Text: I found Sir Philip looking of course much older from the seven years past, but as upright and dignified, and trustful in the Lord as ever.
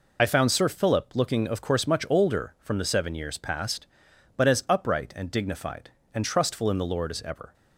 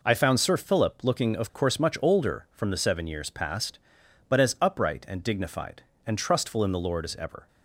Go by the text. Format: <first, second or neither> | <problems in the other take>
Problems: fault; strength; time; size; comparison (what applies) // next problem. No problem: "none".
second | loses the start of "I"; at 0.1 s; 50 ms